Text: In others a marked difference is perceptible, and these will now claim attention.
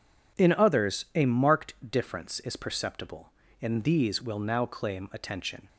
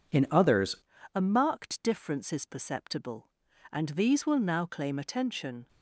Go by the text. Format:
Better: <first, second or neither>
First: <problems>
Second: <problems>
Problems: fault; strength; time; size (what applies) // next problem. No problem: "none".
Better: first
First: none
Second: changes voice at "a"; from 1.1 s on; 4.5 s long